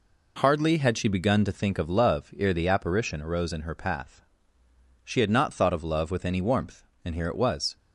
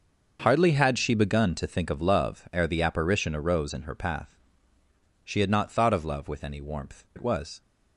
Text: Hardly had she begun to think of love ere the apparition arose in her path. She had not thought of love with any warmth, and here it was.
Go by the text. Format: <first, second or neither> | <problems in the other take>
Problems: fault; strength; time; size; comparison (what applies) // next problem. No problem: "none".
first | starts louder than the rest; noticeable; until 1.4 s; 6 dB // skips "and here"; at 7.1 s